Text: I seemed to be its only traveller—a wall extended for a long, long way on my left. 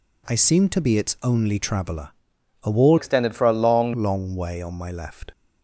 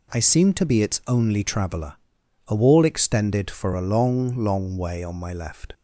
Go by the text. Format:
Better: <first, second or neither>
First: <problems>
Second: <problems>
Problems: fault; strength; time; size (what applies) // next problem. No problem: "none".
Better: second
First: changes voice from "extended" to "long"; from 2.9 to 3.9 s; 1.0 s long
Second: none